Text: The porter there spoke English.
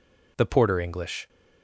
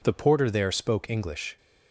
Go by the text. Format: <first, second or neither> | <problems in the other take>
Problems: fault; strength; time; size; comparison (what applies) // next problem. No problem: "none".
second | skips "there spoke"; at 0.8 s